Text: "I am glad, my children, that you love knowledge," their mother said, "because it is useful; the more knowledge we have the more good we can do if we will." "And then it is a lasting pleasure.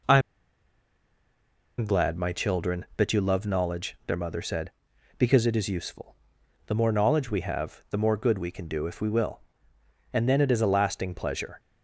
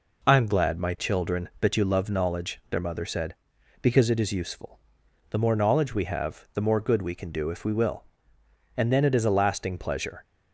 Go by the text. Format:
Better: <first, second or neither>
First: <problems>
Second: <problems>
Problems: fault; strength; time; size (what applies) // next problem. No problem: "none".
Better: second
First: pauses between "I" and "am"; strong; at 0.1 s; 1.5 s long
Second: none